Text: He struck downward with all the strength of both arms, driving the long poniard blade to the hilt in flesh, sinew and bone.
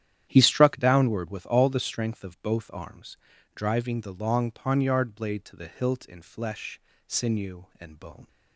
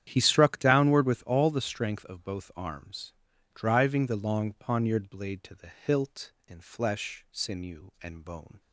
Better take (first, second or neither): neither